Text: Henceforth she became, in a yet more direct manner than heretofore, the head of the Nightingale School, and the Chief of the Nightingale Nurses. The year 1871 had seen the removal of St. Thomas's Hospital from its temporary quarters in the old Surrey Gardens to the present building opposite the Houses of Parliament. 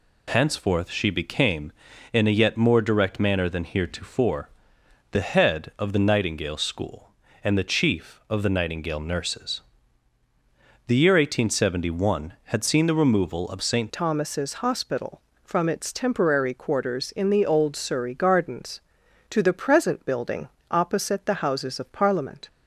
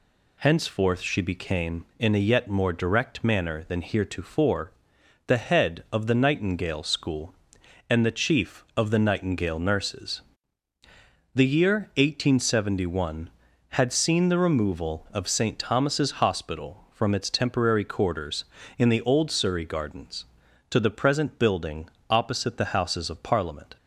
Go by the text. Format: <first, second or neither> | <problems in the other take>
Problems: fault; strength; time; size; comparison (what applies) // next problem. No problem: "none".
second | changes voice at "Thomas's"; from 13.9 s on; 8.5 s long // pauses between "building" and "opposite"; slight; at 20.4 s; 0.22 s long; slight in the second